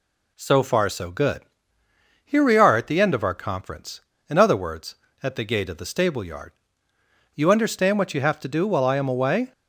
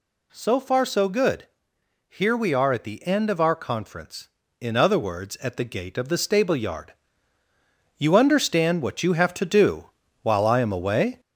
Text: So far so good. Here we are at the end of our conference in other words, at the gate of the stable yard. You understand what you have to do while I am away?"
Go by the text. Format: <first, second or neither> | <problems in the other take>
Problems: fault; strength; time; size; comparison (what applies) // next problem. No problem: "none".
first | gets louder; noticeable; throughout; 4 dB // pauses between "do" and "while"; slight; at 9.8 s; 0.36 s long